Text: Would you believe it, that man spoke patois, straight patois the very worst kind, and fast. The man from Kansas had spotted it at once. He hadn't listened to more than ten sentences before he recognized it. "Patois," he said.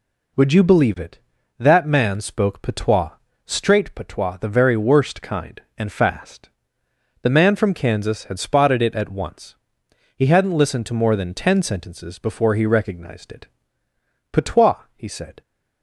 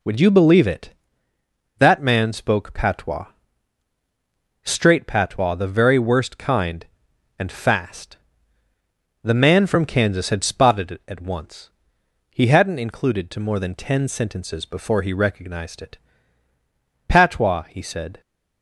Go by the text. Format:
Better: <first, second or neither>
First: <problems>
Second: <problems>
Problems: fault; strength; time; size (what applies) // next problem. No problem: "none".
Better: first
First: none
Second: says "included" for "listened"; at 12.7 s